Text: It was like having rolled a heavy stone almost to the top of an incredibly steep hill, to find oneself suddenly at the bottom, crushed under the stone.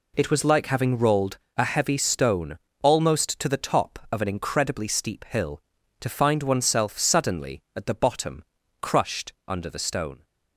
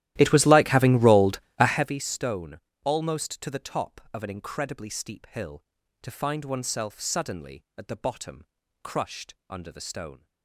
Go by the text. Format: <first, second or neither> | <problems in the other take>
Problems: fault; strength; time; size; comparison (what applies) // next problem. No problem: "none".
first | starts louder than the rest; strong; until 2.0 s; 14 dB // pauses between "rolled" and "a"; slight; at 1.4 s; 0.18 s long; slight in the first // pauses between "stone" and "almost"; slight; at 2.5 s; 0.26 s long; slight in the first